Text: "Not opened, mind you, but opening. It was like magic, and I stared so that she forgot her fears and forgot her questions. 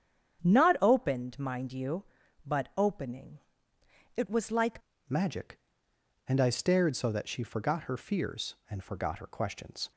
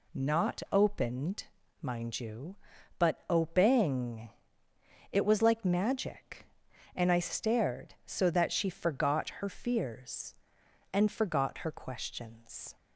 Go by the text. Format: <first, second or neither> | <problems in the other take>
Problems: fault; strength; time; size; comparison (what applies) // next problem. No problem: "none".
second | starts louder than the rest; strong; until 1.4 s; 8.5 dB // changes voice at "magic"; from 5.0 s on; 4.9 s long